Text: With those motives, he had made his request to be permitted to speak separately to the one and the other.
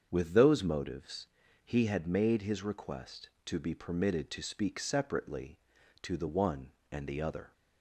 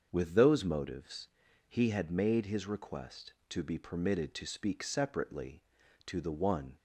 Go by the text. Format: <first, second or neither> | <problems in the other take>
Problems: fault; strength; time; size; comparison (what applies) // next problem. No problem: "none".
first | starts louder than the rest; until 1.1 s; 6.5 dB; strong in the first // stops before "and the other"; at 6.7 s